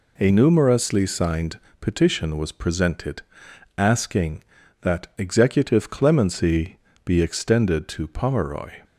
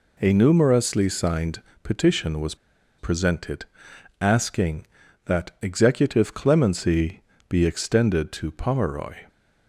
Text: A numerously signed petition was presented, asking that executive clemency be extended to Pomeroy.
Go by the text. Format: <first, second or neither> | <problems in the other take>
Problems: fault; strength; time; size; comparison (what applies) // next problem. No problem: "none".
first | pauses between "signed" and "petition"; slight; at 1.6 s; 0.22 s long; slight in the first // pauses between "was" and "presented"; at 2.5 s; 0.43 s long // pauses between "clemency" and "be"; slight; at 7.2 s; 0.26 s long; slight in the first